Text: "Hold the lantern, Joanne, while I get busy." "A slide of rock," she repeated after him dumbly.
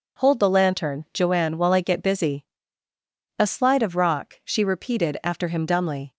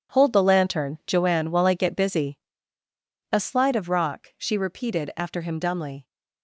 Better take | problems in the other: first | gets quieter; strong; throughout; 12 dB

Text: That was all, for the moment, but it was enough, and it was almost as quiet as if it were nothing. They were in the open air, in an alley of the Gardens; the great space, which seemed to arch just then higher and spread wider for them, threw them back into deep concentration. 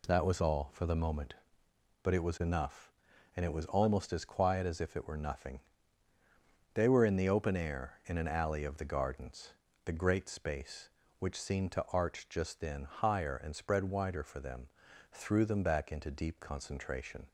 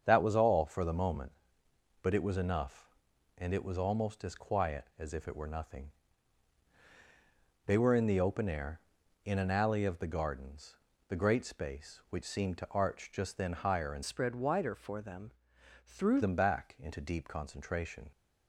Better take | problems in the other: first | starts louder than the rest; strong; until 1.0 s; 7 dB // changes voice from "spread" to "threw"; from 14.0 to 16.2 s; 2.2 s long

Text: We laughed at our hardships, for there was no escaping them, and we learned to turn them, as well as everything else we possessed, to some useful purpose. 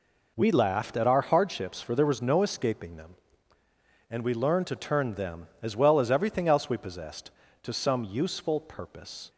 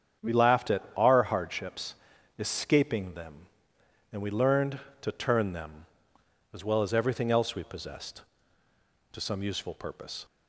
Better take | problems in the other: first | starts louder than the rest; strong; until 1.3 s; 8 dB // skips "for there was no"; at 2.1 s

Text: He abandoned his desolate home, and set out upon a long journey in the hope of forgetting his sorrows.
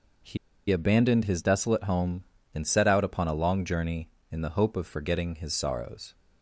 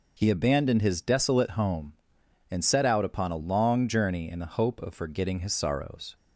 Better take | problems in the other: second | pauses between "He" and "abandoned"; slight; at 0.3 s; 0.32 s long

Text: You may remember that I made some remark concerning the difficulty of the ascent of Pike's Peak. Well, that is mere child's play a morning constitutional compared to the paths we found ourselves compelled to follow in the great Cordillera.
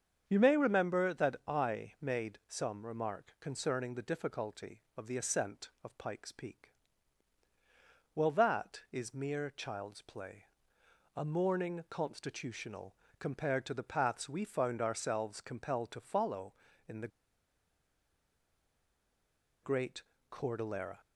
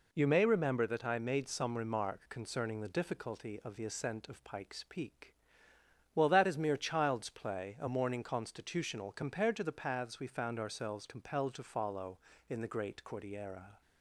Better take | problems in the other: second | starts louder than the rest; strong; until 1.2 s; 7.5 dB // pauses between "play" and "a"; noticeable; at 10.4 s; 0.72 s long // pauses between "constitutional" and "compared"; slight; at 12.9 s; 0.26 s long // pauses between "the" and "great"; strong; at 17.0 s; 2.5 s long // pauses between "great" and "Cordillera"; slight; at 20.0 s; 0.30 s long

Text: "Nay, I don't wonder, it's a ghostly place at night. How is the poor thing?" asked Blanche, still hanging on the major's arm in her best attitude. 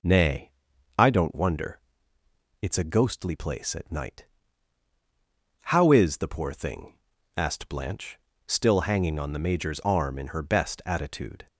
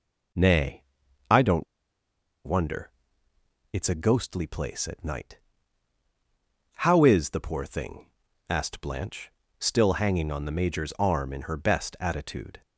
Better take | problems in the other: first | pauses between "don't" and "wonder"; noticeable; at 1.6 s; 0.80 s long

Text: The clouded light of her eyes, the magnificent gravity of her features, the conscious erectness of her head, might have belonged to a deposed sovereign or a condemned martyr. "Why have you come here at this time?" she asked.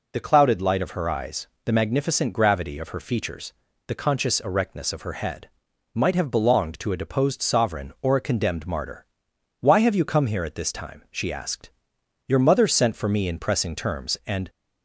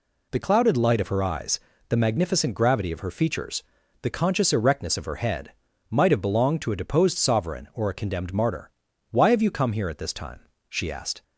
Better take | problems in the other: second | goes on to say "Your mother sent for me in pressing terms and"; strong; from 12.2 s on; 2.2 s long

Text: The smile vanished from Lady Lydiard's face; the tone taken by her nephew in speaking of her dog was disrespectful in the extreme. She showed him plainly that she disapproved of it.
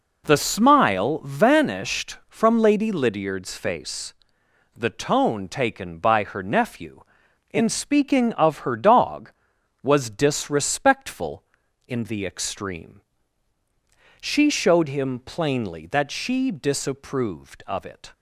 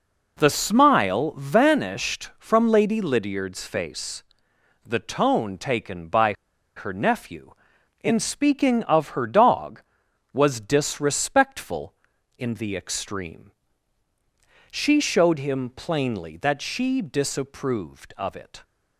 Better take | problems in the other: first | pauses between "by" and "her"; at 6.3 s; 0.42 s long

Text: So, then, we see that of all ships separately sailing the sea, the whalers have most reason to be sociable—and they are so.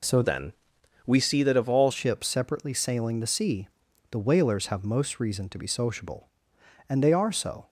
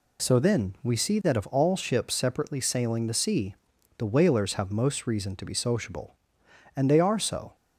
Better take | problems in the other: second | changes voice from "then" to "all"; from 0.2 to 1.9 s; 1.7 s long

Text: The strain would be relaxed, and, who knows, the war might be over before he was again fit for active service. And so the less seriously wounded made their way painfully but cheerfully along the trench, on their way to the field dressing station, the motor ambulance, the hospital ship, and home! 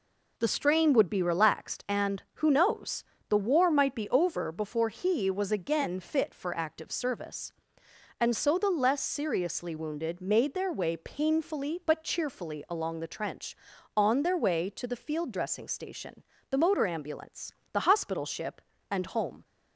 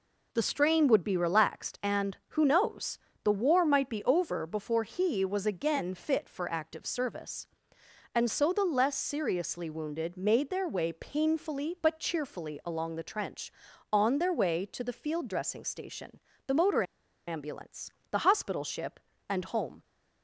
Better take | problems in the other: first | pauses between "motor" and "ambulance"; at 16.8 s; 0.44 s long

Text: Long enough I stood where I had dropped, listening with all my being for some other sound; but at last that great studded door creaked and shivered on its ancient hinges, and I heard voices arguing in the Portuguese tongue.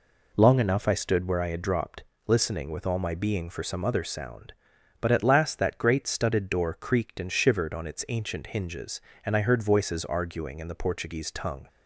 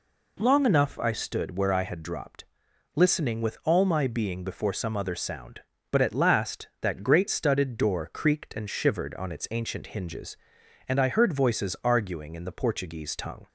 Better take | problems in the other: first | says "before" for "for"; at 4.4 s

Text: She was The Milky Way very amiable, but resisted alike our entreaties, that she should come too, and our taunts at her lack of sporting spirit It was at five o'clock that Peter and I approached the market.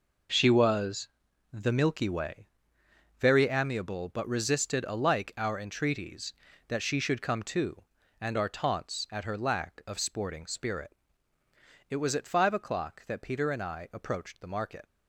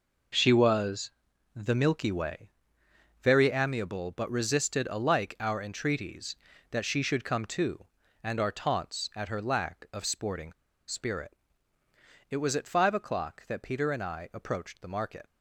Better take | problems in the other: first | pauses between "was" and "The"; at 1.1 s; 0.44 s long; also in the first // pauses between "Way" and "very"; noticeable; at 2.4 s; 0.72 s long; noticeable in the first // pauses between "sporting" and "spirit"; at 10.5 s; 0.36 s long // pauses between "spirit" and "It"; noticeable; at 11.3 s; 0.98 s long; noticeable in the first

